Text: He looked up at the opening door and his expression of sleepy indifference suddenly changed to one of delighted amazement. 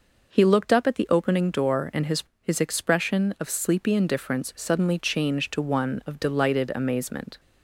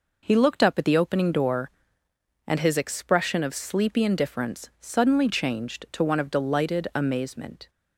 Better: second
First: says "his" twice; at 2.4 s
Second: none

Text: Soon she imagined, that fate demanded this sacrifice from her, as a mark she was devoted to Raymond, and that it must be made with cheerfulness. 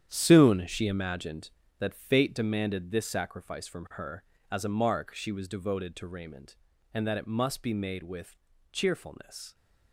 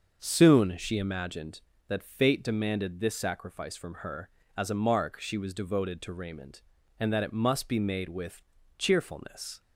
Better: second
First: gets quieter; strong; throughout; 10.5 dB // starts louder than the rest; strong; until 1.1 s; 9.5 dB // pauses between "with" and "cheerfulness"; slight; at 8.3 s; 0.34 s long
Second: starts louder than the rest; until 1.2 s; 6.5 dB // pauses between "with" and "cheerfulness"; slight; at 8.4 s; 0.34 s long

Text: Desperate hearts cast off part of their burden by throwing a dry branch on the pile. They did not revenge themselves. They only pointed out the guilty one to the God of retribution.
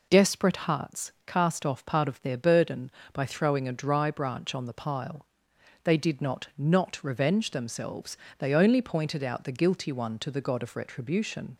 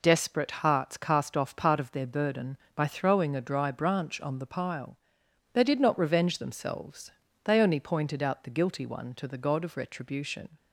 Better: second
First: says "not" twice; at 6.5 s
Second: none

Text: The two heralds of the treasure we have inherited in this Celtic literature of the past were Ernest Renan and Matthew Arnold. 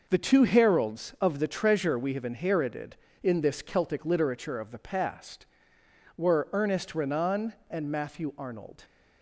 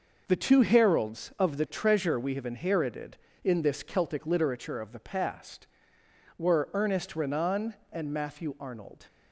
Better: neither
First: none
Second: none

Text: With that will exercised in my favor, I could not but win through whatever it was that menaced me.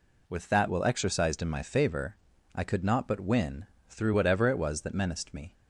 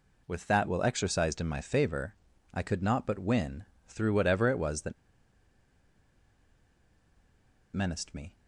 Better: first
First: pauses between "win" and "through"; slight; at 3.6 s; 0.22 s long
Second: pauses between "win" and "through"; slight; at 3.6 s; 0.22 s long // pauses between "that" and "menaced"; strong; at 4.9 s; 2.8 s long

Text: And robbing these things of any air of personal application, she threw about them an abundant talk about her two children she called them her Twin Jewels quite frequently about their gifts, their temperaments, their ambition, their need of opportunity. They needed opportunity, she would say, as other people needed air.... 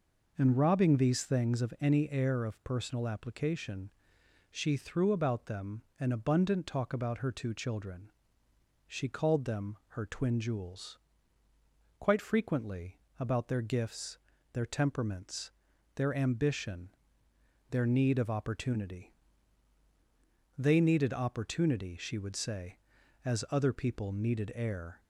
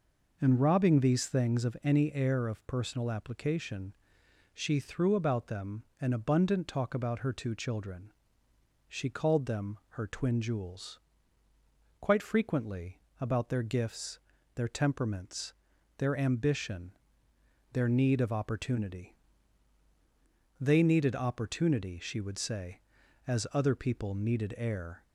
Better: neither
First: pauses between "them" and "an"; slight; at 5.8 s; 0.16 s long // pauses between "children" and "she"; noticeable; at 8.0 s; 0.78 s long // pauses between "Jewels" and "quite"; at 10.9 s; 1.0 s long // pauses between "frequently" and "about"; slight; at 12.9 s; 0.20 s long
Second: pauses between "them" and "an"; slight; at 5.8 s; 0.16 s long // pauses between "children" and "she"; noticeable; at 8.1 s; 0.78 s long // pauses between "Jewels" and "quite"; at 11.0 s; 1.0 s long // pauses between "frequently" and "about"; slight; at 13.0 s; 0.20 s long

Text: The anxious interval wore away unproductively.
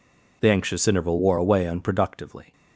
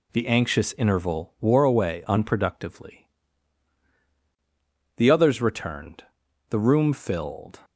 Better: first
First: none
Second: goes on to say "The others returned the room filled"; strong; from 4.9 s on; 2.6 s long

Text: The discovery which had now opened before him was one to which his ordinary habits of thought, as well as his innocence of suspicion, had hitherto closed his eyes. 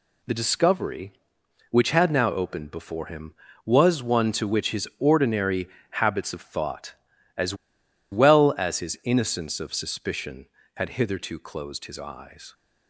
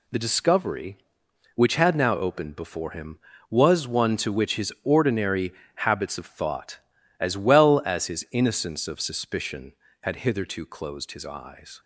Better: second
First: pauses between "ordinary" and "habits"; slight; at 5.6 s; 0.22 s long // pauses between "as" and "well"; noticeable; at 7.5 s; 0.57 s long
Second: pauses between "ordinary" and "habits"; slight; at 5.5 s; 0.22 s long

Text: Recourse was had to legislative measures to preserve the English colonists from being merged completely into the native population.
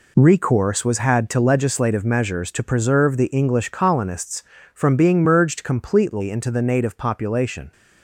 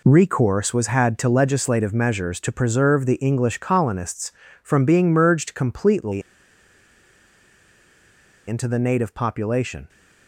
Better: first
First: none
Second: pauses between "completely" and "into"; strong; at 6.2 s; 2.2 s long

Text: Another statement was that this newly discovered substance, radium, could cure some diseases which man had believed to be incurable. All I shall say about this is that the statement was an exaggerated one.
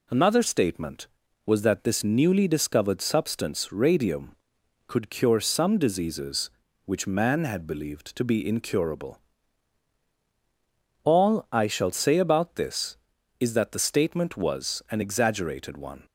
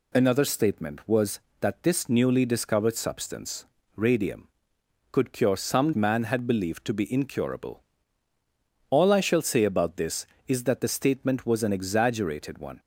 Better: first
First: none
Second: skips "diseases which"; at 5.9 s

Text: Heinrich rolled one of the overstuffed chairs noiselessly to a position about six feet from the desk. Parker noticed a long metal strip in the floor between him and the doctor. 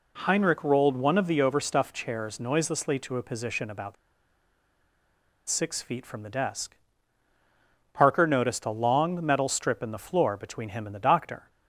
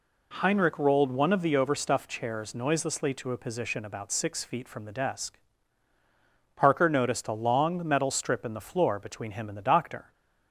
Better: second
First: pauses between "about" and "six"; strong; at 3.9 s; 1.5 s long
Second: none

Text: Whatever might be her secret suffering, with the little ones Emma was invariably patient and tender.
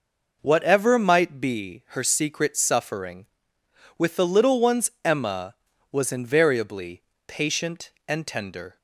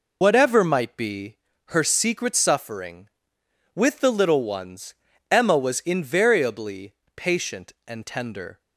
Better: first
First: pauses between "invariably" and "patient"; slight; at 7.0 s; 0.26 s long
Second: loses the start of "Whatever"; at 0.2 s; 80 ms // pauses between "be" and "her"; slight; at 1.3 s; 0.30 s long // pauses between "ones" and "Emma"; at 4.9 s; 0.38 s long // pauses between "invariably" and "patient"; slight; at 6.9 s; 0.22 s long

